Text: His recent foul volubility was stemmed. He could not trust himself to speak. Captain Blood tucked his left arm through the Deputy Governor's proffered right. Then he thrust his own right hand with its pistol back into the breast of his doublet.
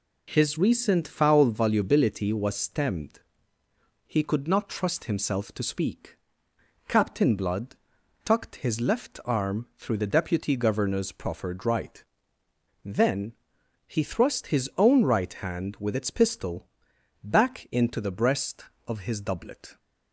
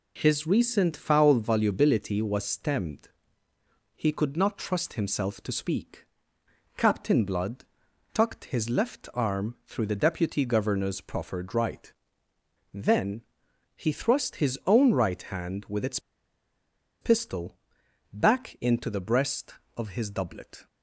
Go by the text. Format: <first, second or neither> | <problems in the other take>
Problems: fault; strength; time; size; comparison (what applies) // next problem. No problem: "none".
first | pauses between "Blood" and "tucked"; noticeable; at 7.6 s; 0.50 s long; noticeable in the first // pauses between "Then" and "he"; noticeable; at 13.2 s; 0.54 s long; noticeable in the first // pauses between "its" and "pistol"; at 15.9 s; 1.0 s long // pauses between "pistol" and "back"; noticeable; at 17.5 s; 0.56 s long; noticeable in the first